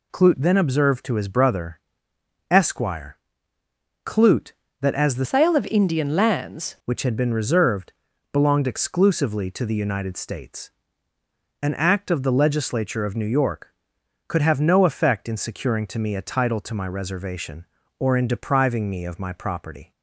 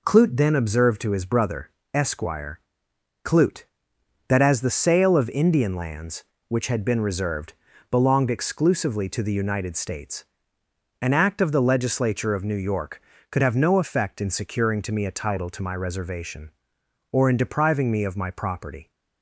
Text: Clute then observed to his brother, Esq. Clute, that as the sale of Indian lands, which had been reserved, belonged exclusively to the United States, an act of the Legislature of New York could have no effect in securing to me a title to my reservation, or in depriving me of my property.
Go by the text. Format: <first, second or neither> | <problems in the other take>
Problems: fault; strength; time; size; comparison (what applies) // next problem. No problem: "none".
second | changes voice from "sale" to "lands"; from 5.2 to 6.7 s; 1.5 s long